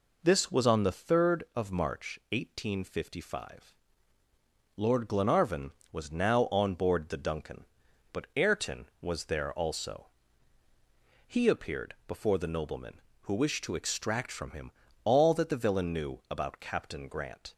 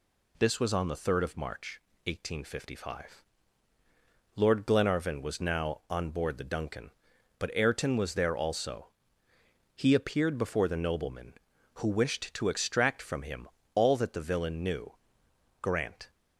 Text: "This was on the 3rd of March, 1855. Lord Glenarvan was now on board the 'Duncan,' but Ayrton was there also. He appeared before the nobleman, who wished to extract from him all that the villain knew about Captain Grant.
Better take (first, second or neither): first